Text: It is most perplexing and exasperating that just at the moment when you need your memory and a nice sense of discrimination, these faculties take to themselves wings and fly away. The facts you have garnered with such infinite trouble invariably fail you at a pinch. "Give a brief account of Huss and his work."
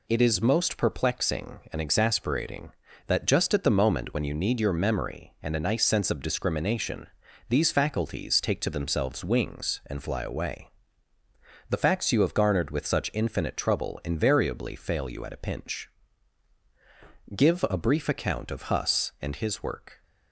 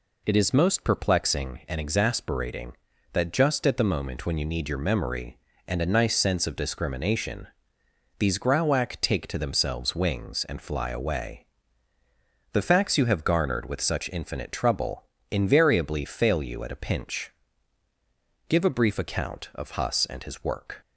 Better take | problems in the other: first | says "grauwack" for "faculties"; at 8.3 s // pauses between "trouble" and "invariably"; slight; at 15.0 s; 0.26 s long

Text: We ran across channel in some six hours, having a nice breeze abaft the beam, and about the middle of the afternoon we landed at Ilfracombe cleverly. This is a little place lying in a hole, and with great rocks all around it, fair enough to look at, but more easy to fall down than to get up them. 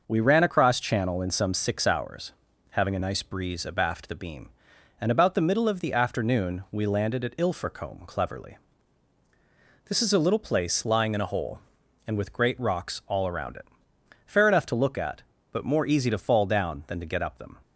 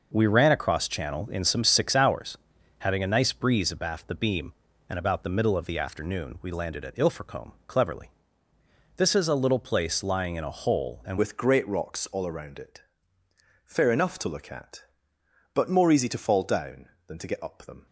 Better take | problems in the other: first | changes voice at "with"; from 11.1 s on; 6.7 s long

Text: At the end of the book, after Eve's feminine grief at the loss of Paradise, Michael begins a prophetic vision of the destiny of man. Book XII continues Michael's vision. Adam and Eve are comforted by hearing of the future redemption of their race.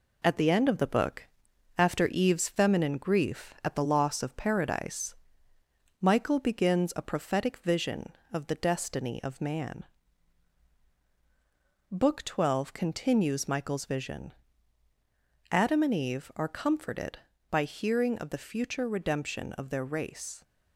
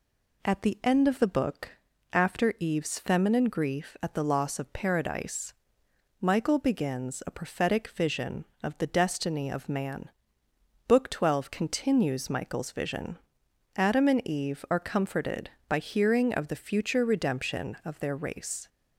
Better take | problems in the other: second | gets quieter; throughout; 3.5 dB

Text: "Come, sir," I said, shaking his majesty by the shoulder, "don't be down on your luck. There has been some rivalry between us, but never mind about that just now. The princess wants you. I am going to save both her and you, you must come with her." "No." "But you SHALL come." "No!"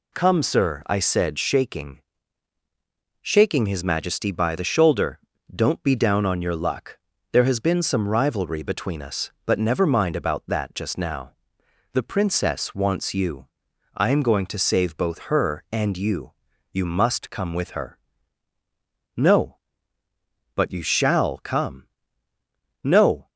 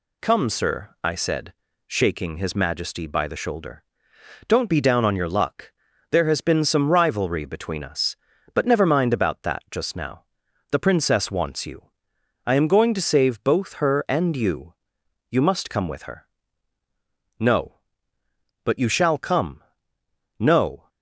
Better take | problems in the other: second | says "shaking" twice; at 3.2 s

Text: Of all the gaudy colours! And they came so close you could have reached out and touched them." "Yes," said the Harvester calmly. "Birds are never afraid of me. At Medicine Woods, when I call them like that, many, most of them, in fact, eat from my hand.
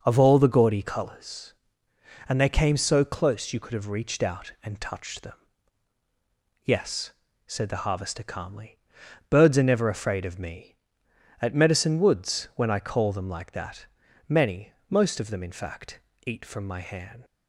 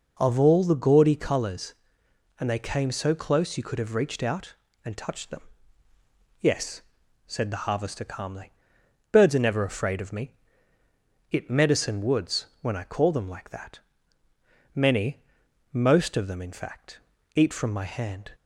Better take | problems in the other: first | says "It" for "At"; at 11.3 s

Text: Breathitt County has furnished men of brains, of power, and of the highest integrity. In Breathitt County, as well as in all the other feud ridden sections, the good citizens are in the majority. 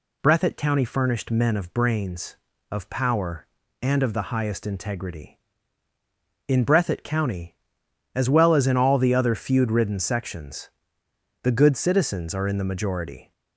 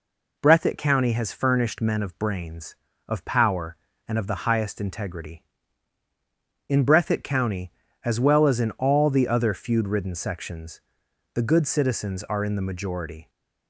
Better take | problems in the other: second | skips "has"; at 0.8 s

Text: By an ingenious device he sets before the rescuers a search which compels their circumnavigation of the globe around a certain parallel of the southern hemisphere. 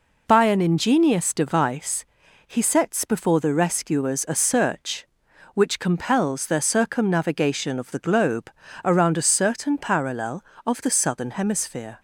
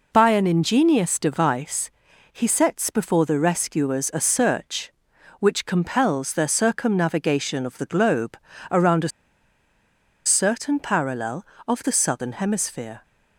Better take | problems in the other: first | pauses between "device" and "he"; at 1.8 s; 0.42 s long; also in the first // pauses between "globe" and "around"; slight; at 8.3 s; 0.34 s long; slight in the first // pauses between "a" and "certain"; at 9.1 s; 1.1 s long

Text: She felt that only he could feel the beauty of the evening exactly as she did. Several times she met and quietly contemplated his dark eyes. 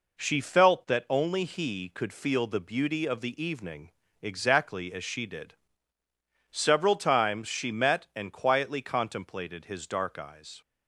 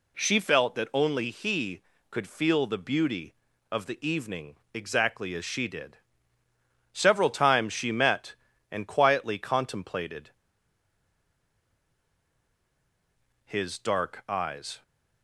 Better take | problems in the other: first | pauses between "evening" and "exactly"; slight; at 4.5 s; 0.18 s long; slight in the first // pauses between "contemplated" and "his"; strong; at 10.2 s; 3.1 s long

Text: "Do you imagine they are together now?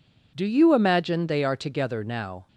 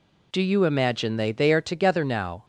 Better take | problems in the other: first | says "they" twice; at 1.3 s

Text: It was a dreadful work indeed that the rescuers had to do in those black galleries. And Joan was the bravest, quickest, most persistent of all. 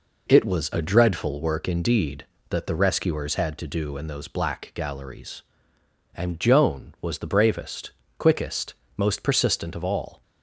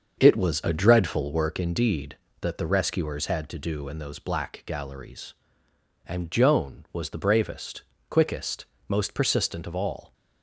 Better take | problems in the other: first | starts louder than the rest; until 1.6 s; 6.5 dB

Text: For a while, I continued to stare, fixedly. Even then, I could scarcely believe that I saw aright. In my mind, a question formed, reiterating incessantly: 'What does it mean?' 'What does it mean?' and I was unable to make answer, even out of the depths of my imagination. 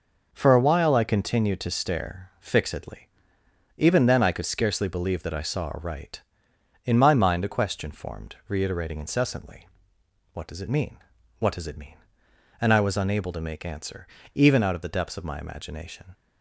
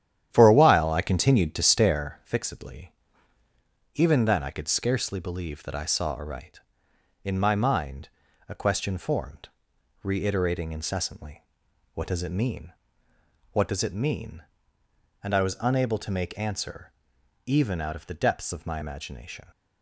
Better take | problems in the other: first | starts louder than the rest; strong; until 2.2 s; 10.5 dB

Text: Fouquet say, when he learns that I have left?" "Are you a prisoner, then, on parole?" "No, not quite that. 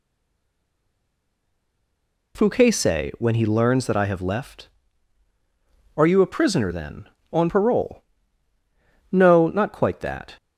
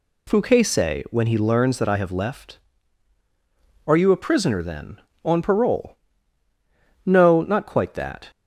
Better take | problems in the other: second | stays silent before the first word; until 2.3 s; 2.3 s long

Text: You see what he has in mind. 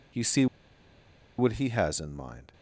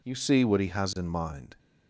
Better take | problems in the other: second | pauses between "see" and "what"; noticeable; at 0.4 s; 0.92 s long

